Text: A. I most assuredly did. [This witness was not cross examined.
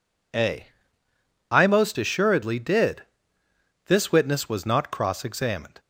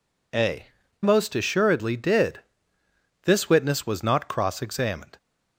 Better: first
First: none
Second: skips "I"; at 0.8 s

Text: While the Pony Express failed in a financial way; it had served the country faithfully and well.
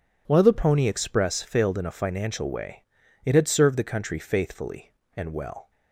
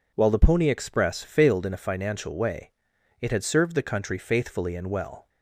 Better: neither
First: none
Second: none

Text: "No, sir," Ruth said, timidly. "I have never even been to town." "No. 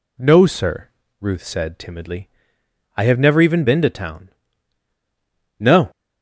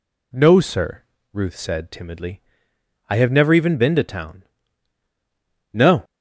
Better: neither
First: none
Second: none

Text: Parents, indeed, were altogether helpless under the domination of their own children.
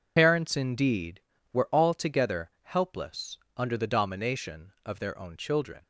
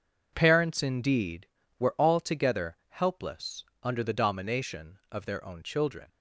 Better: second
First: loses the start of "Parents"; at 0.1 s; 85 ms // pauses between "helpless" and "under"; slight; at 3.3 s; 0.20 s long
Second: pauses between "helpless" and "under"; slight; at 3.6 s; 0.20 s long

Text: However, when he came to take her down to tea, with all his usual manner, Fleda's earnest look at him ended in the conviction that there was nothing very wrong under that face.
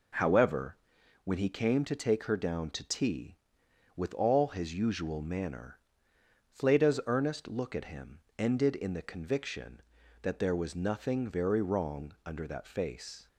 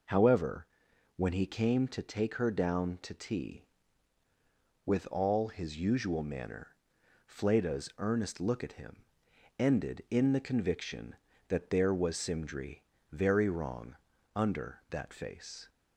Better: first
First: pauses between "him" and "ended"; slight; at 8.1 s; 0.18 s long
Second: pauses between "him" and "ended"; noticeable; at 9.0 s; 0.54 s long // says "simdry" for "nothing"; at 12.1 s // pauses between "wrong" and "under"; at 13.9 s; 0.38 s long

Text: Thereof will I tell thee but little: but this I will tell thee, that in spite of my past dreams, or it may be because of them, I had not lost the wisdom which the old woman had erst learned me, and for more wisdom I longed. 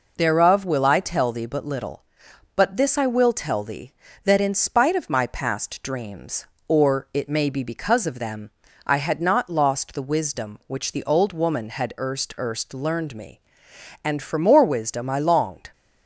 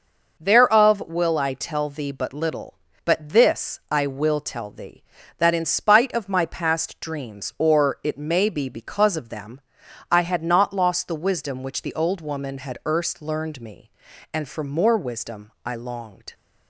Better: second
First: says "erst" twice; at 12.3 s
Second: none

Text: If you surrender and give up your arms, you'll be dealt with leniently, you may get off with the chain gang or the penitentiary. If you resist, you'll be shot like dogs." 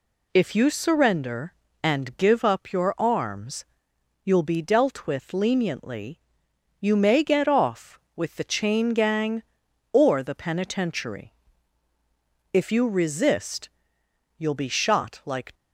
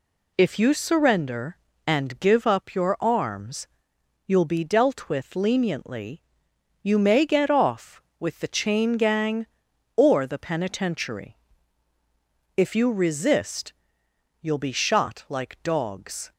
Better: second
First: stops before "dogs"; at 15.5 s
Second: none

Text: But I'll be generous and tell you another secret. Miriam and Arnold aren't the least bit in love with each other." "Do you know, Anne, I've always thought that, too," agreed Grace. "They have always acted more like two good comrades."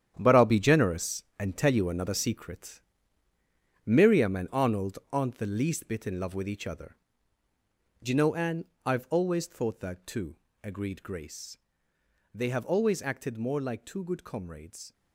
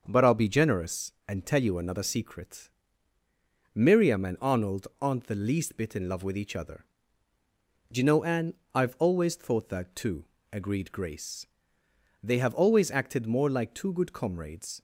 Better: second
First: gets quieter; strong; throughout; 11 dB // starts louder than the rest; strong; until 1.1 s; 9.5 dB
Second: starts louder than the rest; until 1.0 s; 6.5 dB

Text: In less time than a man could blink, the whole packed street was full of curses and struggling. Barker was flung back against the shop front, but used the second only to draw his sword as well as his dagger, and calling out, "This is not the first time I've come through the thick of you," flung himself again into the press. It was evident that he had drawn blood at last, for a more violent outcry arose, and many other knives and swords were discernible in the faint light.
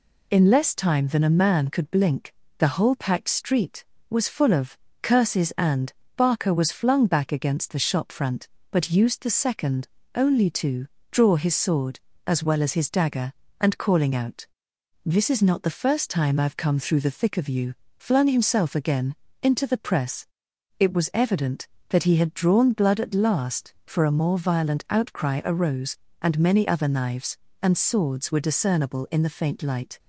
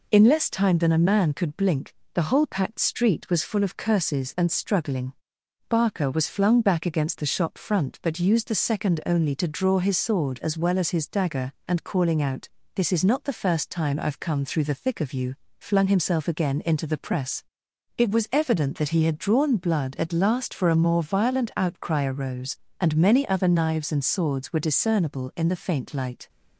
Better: second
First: pauses between "of" and "curses"; slight; at 4.7 s; 0.26 s long // skips "struggling"; at 6.0 s // pauses between "second" and "only"; slight; at 9.8 s; 0.26 s long // pauses between "to" and "draw"; slight; at 10.8 s; 0.24 s long // pauses between "again" and "into"; slight; at 19.1 s; 0.26 s long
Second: none

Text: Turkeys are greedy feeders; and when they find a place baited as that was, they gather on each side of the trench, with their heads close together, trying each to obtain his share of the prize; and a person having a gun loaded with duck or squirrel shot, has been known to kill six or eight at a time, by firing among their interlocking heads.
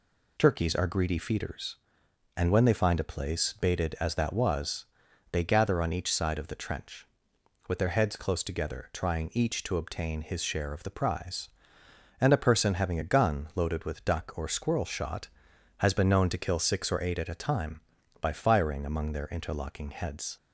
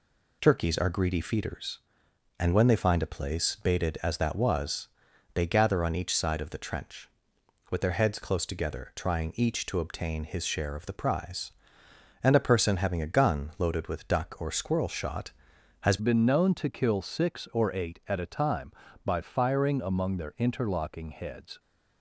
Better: first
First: none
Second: changes voice at "been"; from 15.9 s on; 5.6 s long

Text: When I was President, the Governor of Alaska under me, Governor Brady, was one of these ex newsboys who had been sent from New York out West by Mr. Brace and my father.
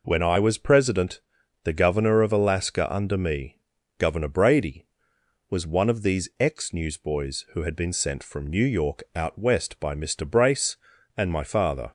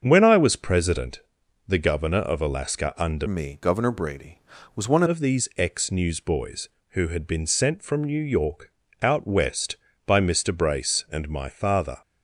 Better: first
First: none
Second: starts louder than the rest; strong; until 1.0 s; 7 dB // changes voice from "me" to "one"; from 3.2 to 5.0 s; 1.8 s long // pauses between "York" and "out"; slight; at 8.7 s; 0.32 s long

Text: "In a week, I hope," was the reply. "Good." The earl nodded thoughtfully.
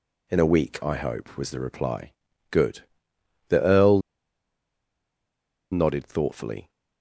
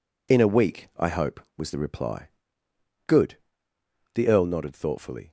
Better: second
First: pauses between "earl" and "nodded"; strong; at 4.0 s; 1.7 s long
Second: none

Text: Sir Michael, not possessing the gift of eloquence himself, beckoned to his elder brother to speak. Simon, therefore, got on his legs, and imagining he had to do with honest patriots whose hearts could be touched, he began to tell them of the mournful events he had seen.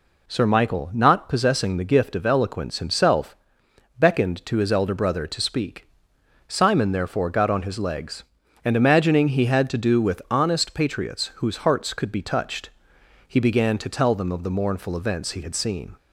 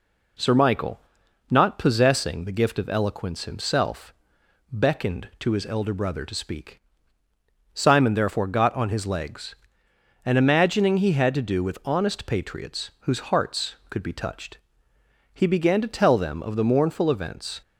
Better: first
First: none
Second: stops before "he had seen"; at 17.6 s

